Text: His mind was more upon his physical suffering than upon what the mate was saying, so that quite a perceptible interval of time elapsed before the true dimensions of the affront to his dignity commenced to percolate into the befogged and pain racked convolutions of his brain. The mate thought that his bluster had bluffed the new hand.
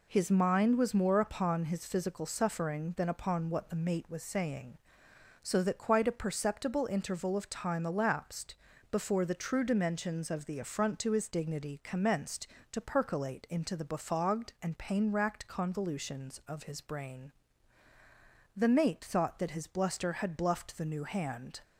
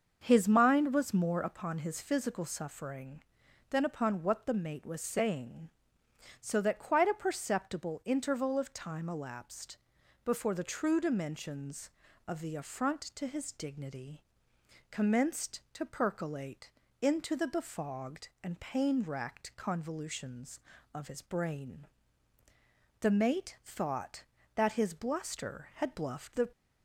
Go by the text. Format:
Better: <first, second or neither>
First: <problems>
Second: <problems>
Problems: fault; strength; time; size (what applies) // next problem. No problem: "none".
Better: first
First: pauses between "elapsed" and "before"; slight; at 8.5 s; 0.36 s long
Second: starts louder than the rest; until 1.2 s; 6.5 dB // pauses between "elapsed" and "before"; noticeable; at 9.7 s; 0.46 s long // pauses between "dignity" and "commenced"; noticeable; at 14.2 s; 0.70 s long // pauses between "percolate" and "into"; slight; at 16.7 s; 0.30 s long // stops before "new hand"; at 26.5 s